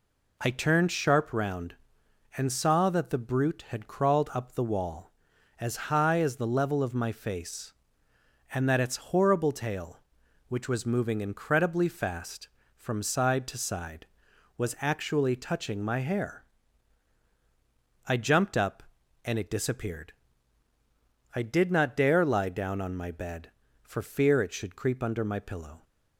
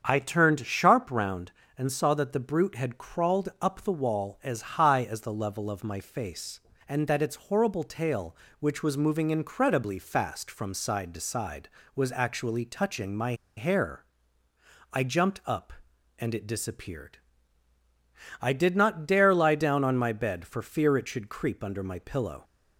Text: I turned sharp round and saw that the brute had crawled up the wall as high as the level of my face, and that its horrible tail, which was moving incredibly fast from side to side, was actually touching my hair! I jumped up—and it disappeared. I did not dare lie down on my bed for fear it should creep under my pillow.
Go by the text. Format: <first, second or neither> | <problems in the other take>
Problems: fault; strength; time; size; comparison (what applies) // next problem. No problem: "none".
first | starts louder than the rest; strong; until 1.0 s; 7.5 dB // pauses between "my" and "hair"; slight; at 13.3 s; 0.22 s long